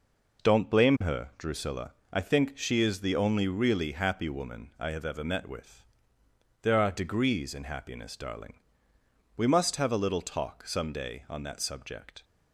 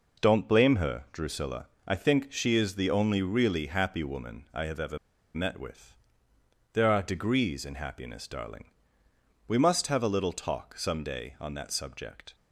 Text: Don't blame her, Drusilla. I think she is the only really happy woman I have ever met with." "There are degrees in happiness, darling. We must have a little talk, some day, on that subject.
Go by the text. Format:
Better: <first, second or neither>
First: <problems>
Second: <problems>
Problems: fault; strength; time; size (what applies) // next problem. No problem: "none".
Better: first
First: none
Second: pauses between "ever" and "met"; at 4.9 s; 0.36 s long